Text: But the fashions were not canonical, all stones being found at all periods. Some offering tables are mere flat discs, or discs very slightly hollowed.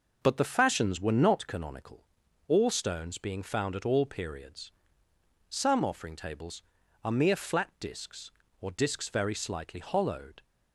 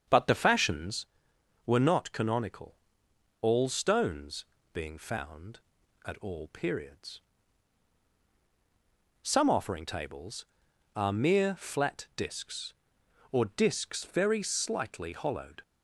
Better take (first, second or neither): first